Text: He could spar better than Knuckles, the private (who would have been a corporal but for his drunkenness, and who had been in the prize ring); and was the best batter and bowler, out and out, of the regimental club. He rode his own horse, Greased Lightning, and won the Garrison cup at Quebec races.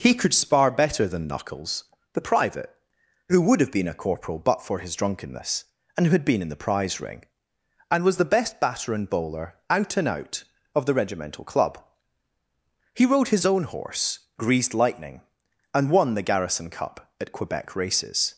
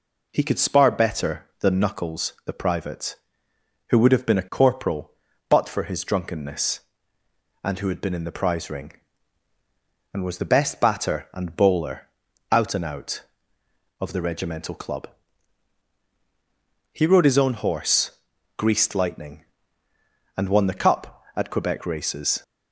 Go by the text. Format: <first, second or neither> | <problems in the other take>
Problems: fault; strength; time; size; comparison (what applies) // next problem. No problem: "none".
first | skips "Garrison"; at 20.7 s